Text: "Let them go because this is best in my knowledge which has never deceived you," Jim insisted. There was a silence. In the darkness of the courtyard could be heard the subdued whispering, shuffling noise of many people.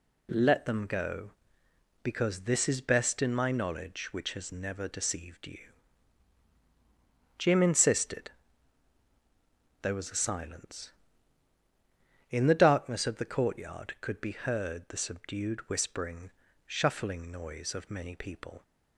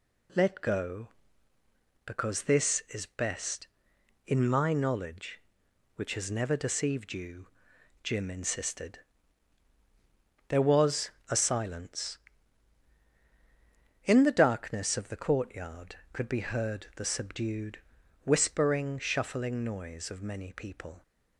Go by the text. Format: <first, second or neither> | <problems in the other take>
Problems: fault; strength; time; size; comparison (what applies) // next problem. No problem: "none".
first | skips "them"; at 0.6 s // pauses between "was" and "a"; slight; at 11.1 s; 0.18 s long // pauses between "subdued" and "whispering"; at 17.7 s; 0.44 s long